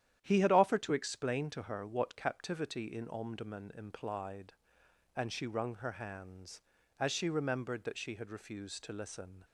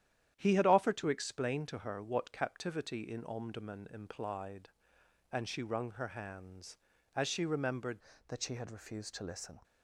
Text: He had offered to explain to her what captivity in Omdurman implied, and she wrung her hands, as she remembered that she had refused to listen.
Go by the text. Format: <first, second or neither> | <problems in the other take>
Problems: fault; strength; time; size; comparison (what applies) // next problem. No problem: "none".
first | starts louder than the rest; strong; until 1.3 s; 10.5 dB; strong in the first // changes voice at "that"; from 8.2 s on; 1.3 s long